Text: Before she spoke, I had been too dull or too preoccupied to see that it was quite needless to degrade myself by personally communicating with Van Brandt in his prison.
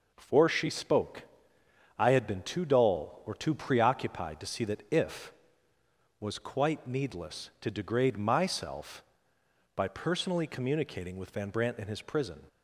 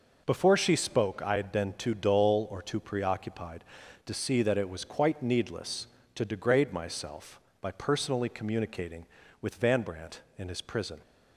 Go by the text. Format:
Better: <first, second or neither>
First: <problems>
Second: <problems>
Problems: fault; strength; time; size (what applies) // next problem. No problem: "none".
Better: second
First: says "if" for "it"; at 4.9 s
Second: none